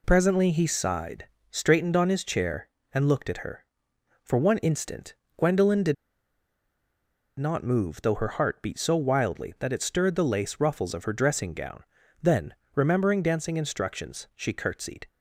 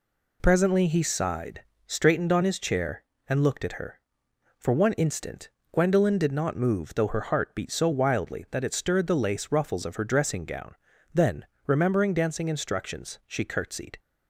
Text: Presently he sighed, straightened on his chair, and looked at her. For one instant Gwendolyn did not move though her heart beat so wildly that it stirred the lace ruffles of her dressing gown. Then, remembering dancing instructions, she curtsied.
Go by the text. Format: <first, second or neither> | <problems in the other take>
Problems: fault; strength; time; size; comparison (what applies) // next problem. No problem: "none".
second | pauses between "instant" and "Gwendolyn"; slight; at 5.1 s; 0.22 s long; slight in the second // pauses between "did" and "not"; strong; at 5.9 s; 1.4 s long